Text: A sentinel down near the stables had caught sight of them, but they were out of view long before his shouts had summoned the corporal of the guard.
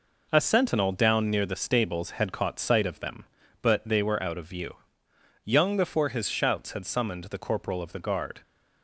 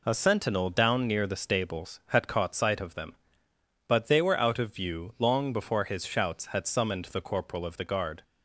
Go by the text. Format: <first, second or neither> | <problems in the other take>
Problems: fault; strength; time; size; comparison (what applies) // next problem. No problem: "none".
second | says "young" for "long"; at 5.4 s